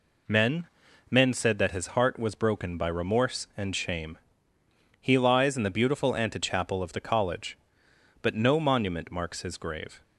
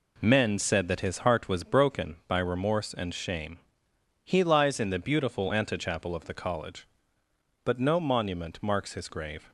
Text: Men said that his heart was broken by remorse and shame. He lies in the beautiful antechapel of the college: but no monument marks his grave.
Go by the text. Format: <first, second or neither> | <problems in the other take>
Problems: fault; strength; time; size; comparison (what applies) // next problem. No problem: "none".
second | says "Men" twice; at 1.1 s